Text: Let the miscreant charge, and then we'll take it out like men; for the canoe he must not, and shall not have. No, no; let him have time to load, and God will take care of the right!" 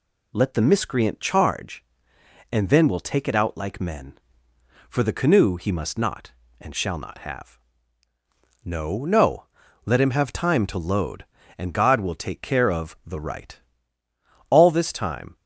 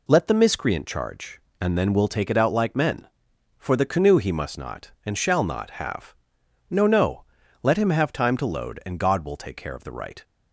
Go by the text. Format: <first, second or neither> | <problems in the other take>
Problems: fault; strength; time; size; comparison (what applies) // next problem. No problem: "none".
second | goes on to say "All this time"; noticeable; from 14.4 s on; 0.86 s long